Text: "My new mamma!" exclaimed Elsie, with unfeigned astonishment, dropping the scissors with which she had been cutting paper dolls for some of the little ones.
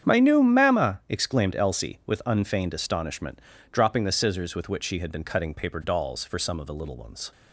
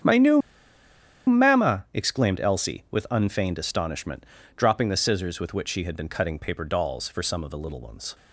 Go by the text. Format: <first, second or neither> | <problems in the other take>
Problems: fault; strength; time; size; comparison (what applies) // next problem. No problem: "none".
first | starts louder than the rest; strong; until 1.9 s; 8 dB; strong in the first // pauses between "new" and "mamma"; noticeable; at 0.4 s; 0.86 s long